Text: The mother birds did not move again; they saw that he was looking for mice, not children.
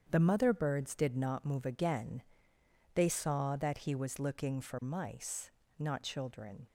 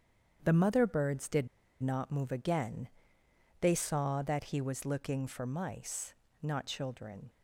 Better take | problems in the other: first | starts louder than the rest; strong; until 1.4 s; 8 dB; strong in the first // pauses between "did" and "not"; slight; at 1.4 s; 0.35 s long

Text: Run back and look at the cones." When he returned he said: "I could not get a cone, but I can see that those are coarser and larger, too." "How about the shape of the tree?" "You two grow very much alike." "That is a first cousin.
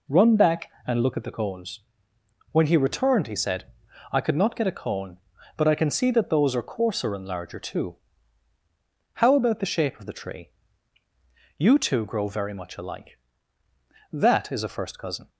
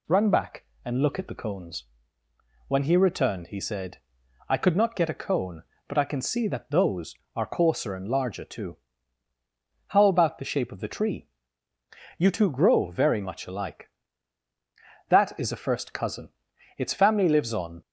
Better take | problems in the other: first | goes on to say "Its family lives on"; noticeable; from 16.7 s on; 1.0 s long

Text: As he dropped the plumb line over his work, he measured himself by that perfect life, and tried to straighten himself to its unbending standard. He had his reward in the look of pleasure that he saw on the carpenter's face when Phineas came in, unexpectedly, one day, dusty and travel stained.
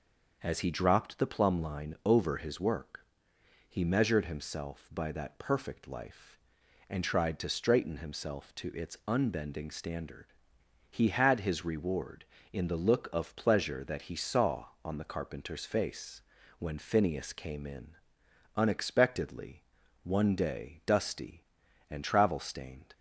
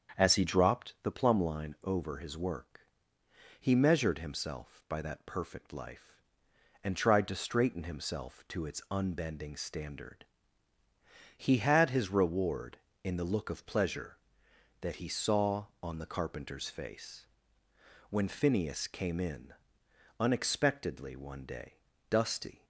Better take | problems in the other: first | starts louder than the rest; strong; until 1.2 s; 7 dB // pauses between "face" and "when"; noticeable; at 17.2 s; 0.84 s long; slight in the first // stops before "and travel stained"; at 22.6 s

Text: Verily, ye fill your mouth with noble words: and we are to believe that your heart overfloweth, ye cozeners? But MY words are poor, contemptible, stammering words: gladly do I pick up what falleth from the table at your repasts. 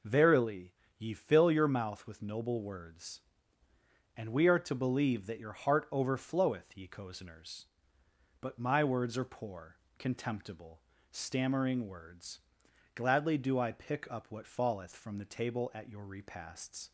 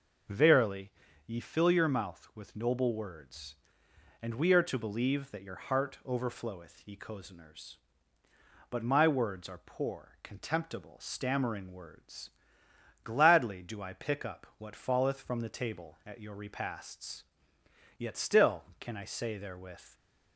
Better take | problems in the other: first | goes on to say "Yet still can I say therewith"; strong; from 17.9 s on; 1.9 s long

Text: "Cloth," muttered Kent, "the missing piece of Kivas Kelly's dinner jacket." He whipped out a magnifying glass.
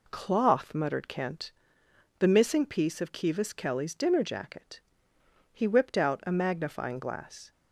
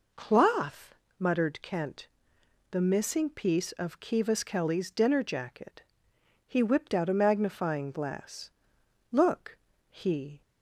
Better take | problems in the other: first | goes on to say "Look he"; noticeable; from 9.1 s on; 1.3 s long

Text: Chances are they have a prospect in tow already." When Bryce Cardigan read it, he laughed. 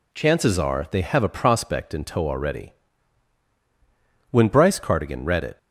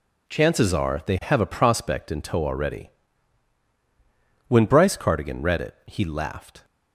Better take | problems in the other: second | stops before "he laughed"; at 5.5 s

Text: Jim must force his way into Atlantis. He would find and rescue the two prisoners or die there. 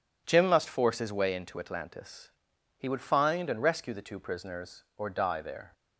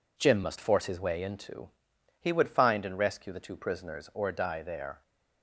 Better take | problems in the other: first | skips "Atlantis"; at 1.9 s

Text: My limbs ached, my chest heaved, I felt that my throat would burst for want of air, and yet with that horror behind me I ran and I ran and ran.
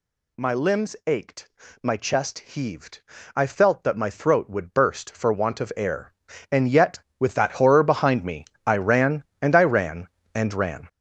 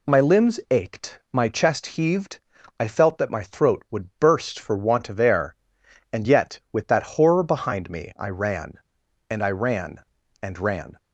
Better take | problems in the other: second | gets louder; strong; throughout; 9 dB // pauses between "me" and "I"; slight; at 8.4 s; 0.20 s long

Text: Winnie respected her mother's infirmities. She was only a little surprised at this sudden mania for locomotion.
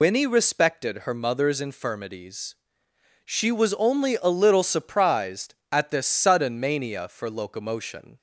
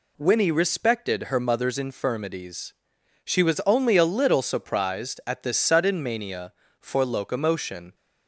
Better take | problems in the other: second | loses the start of "Winnie"; at 0.0 s; 70 ms

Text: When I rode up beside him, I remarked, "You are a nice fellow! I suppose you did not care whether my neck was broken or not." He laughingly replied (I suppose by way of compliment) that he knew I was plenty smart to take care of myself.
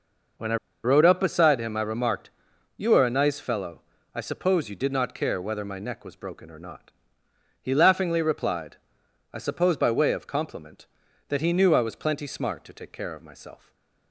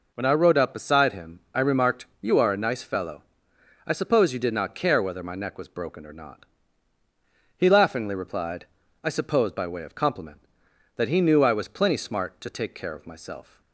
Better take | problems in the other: second | pauses between "I" and "rode"; slight; at 0.5 s; 0.28 s long // stays silent after the last word; slight; from 13.5 s on; 0.6 s long

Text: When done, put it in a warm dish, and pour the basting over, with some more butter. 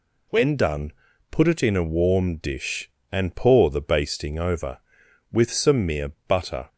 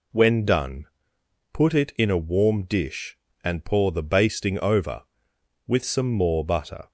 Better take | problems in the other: second | says "mere" for "more"; at 5.8 s

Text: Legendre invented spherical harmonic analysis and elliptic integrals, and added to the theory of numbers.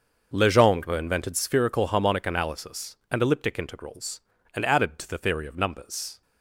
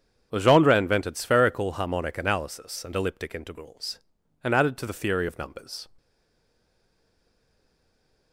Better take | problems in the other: first | starts louder than the rest; strong; until 1.3 s; 8 dB; also in the first // stays silent after the last word; from 5.9 s on; 2.4 s long

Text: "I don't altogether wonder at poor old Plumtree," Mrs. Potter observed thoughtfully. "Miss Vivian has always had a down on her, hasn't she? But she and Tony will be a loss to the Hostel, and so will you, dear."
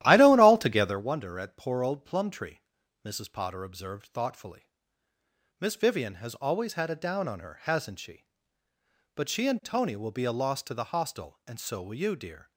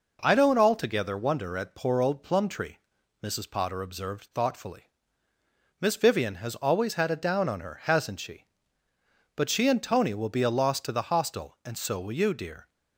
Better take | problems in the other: second | starts louder than the rest; strong; until 1.1 s; 13 dB

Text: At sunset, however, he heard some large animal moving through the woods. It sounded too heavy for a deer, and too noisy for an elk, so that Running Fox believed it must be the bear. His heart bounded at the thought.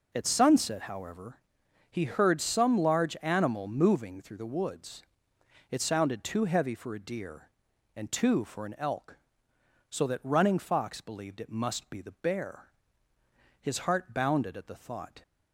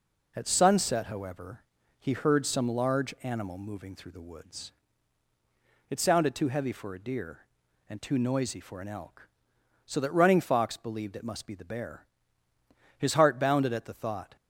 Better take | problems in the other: second | skips "noisy"; at 8.4 s

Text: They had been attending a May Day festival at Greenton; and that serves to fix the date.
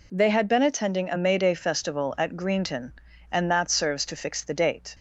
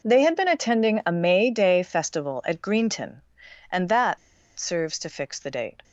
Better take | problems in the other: first | pauses between "that" and "serves"; at 4.1 s; 0.39 s long

